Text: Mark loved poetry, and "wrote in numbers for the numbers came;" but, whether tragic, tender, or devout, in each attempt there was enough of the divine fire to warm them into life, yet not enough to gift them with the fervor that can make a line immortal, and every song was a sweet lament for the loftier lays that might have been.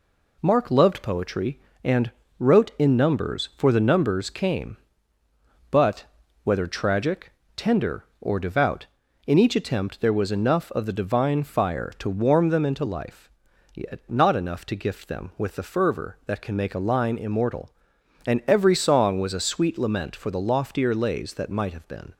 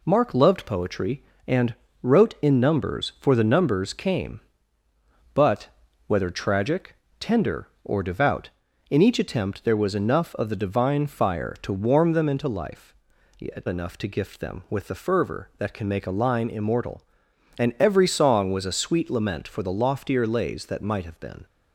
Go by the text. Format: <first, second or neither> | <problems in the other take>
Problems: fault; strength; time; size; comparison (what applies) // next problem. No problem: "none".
first | pauses between "and" and "wrote"; slight; at 1.7 s; 0.26 s long; slight in the first // skips "not"; at 13.6 s